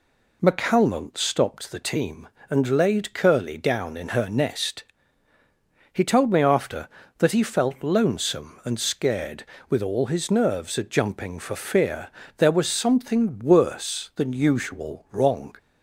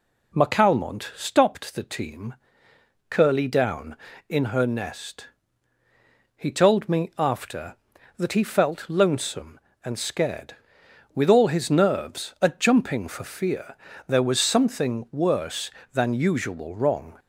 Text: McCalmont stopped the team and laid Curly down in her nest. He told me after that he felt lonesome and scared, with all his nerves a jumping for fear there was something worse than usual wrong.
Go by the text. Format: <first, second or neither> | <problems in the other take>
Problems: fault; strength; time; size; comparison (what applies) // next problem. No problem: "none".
first | skips "and laid"; at 2.7 s // pauses between "fear" and "there"; slight; at 13.7 s; 0.32 s long; slight in the first